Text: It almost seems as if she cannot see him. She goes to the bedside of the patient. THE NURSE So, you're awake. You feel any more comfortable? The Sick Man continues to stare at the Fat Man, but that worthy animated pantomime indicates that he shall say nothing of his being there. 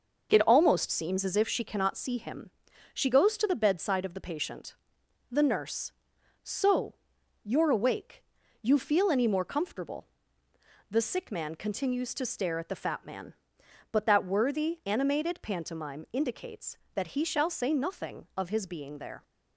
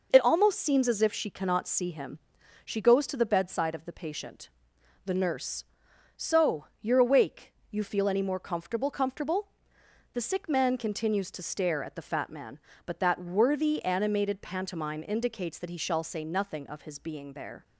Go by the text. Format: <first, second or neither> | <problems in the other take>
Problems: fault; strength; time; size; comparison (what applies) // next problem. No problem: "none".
first | says "comfortable" twice; at 8.9 s